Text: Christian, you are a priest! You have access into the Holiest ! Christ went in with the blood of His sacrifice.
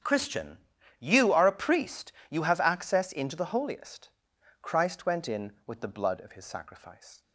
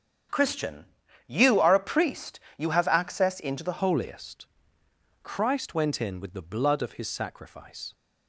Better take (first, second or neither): first